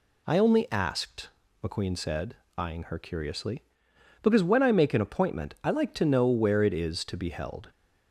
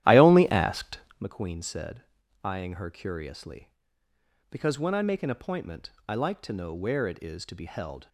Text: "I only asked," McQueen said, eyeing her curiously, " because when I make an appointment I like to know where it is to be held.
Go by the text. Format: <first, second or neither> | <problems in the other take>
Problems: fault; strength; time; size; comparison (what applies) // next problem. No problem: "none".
first | starts louder than the rest; strong; until 1.3 s; 13 dB // pauses between "appointment" and "I"; slight; at 5.9 s; 0.16 s long